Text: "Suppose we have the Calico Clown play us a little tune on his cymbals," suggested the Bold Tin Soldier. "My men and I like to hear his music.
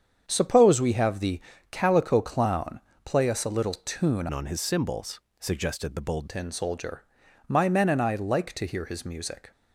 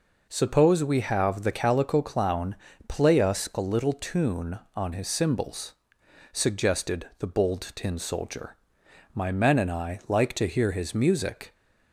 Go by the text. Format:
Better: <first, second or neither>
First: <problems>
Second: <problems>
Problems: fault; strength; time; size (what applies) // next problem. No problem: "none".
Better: second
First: starts louder than the rest; strong; until 1.2 s; 7.5 dB // pauses between "the" and "Calico"; slight; at 1.4 s; 0.30 s long // pauses between "Clown" and "play"; slight; at 2.8 s; 0.24 s long // changes voice from "on" to "Bold"; from 4.3 to 6.2 s; 1.9 s long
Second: pauses between "Clown" and "play"; slight; at 2.5 s; 0.32 s long